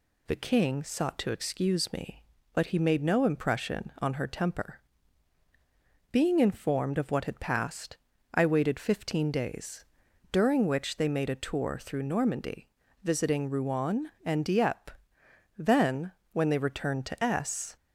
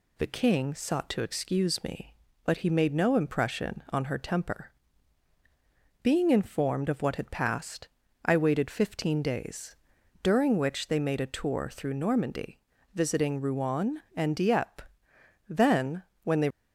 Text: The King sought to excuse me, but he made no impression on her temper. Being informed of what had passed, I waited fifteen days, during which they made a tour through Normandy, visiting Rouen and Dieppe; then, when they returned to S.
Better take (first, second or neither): first